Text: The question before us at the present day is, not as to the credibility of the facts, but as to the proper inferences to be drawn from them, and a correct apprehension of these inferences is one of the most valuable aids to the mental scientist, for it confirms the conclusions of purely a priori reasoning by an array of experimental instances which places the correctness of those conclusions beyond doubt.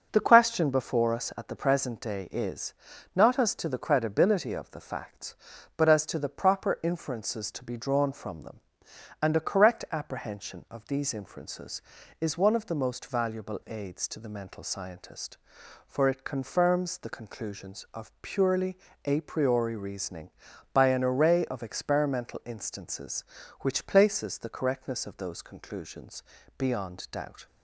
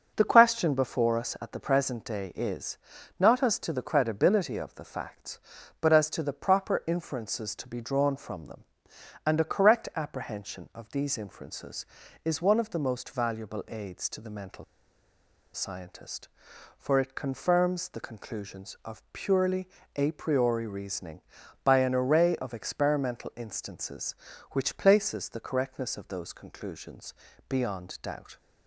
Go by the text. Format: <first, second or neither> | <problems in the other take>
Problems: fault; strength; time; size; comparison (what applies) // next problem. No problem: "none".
first | pauses between "mental" and "scientist"; noticeable; at 14.6 s; 0.90 s long // pauses between "purely" and "a"; slight; at 19.6 s; 0.30 s long; slight in the first // pauses between "conclusions" and "beyond"; slight; at 27.1 s; 0.36 s long; slight in the first